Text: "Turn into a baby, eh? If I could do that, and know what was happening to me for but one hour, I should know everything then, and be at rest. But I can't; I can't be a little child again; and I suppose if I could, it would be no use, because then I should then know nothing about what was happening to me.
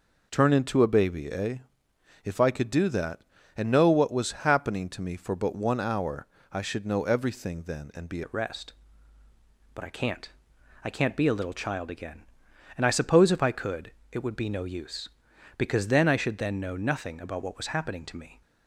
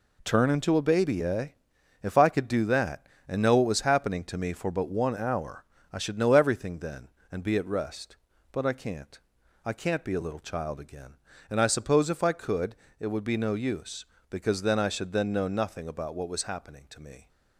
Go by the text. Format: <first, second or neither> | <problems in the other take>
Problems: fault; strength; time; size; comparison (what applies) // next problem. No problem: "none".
second | changes voice at "at"; from 8.2 s on; 10.2 s long